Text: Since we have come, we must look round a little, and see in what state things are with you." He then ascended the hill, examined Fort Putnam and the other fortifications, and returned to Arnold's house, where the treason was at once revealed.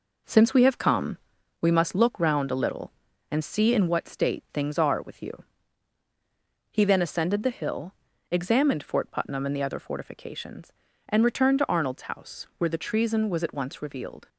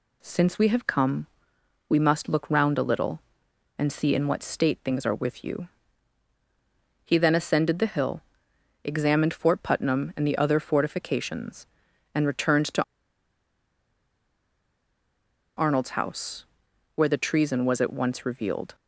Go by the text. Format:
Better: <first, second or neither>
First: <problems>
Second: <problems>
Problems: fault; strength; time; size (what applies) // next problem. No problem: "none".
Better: first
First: none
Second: pauses between "to" and "Arnold's"; strong; at 12.8 s; 2.7 s long